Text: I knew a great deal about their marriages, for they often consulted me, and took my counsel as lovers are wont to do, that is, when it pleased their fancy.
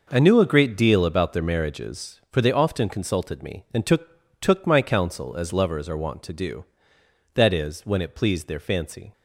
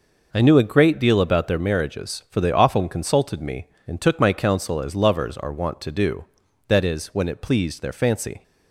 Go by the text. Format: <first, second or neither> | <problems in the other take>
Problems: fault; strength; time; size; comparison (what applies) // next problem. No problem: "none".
second | says "took" twice; at 4.4 s